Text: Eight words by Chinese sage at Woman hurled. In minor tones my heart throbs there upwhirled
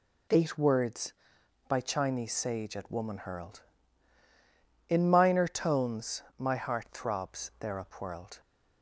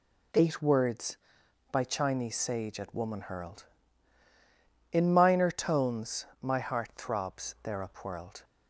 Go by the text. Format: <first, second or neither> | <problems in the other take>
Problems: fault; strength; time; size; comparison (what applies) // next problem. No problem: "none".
neither | none